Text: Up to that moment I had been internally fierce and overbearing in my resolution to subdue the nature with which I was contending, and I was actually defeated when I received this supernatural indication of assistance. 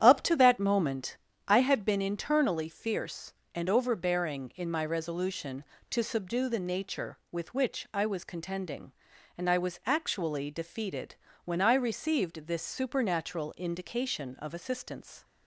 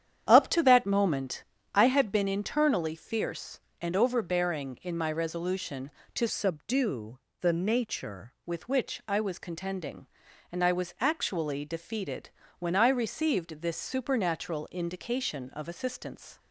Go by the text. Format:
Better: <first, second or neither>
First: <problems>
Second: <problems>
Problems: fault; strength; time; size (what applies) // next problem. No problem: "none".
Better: first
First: starts louder than the rest; strong; until 1.0 s; 9.5 dB // pauses between "moment" and "I"; slight; at 1.1 s; 0.30 s long // pauses between "defeated" and "when"; slight; at 11.1 s; 0.30 s long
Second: starts louder than the rest; strong; until 1.3 s; 9.5 dB // pauses between "moment" and "I"; slight; at 1.4 s; 0.30 s long // changes voice from "subdue" to "nature"; from 6.2 to 8.3 s; 2.1 s long // pauses between "subdue" and "the"; slight; at 7.1 s; 0.22 s long // pauses between "defeated" and "when"; slight; at 12.2 s; 0.30 s long